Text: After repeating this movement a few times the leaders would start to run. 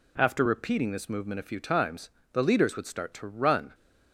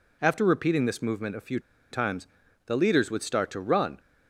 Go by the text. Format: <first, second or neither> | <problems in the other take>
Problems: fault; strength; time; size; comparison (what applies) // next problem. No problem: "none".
first | pauses between "few" and "times"; slight; at 1.5 s; 0.32 s long // pauses between "times" and "the"; at 2.2 s; 0.40 s long; slight in the first